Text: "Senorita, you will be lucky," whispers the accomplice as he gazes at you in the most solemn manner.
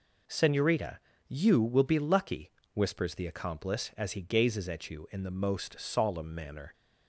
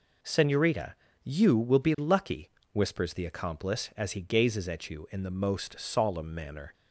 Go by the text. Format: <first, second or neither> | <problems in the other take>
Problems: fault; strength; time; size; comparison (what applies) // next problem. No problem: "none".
neither | none